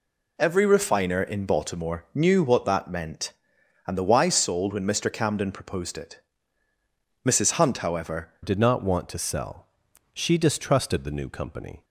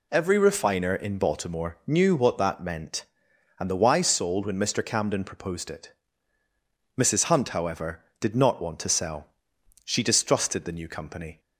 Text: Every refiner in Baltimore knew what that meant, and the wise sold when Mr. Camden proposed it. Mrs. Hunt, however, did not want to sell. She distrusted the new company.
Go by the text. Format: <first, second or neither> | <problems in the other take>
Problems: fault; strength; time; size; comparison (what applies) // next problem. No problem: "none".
second | changes voice at "did"; from 8.4 s on; 3.4 s long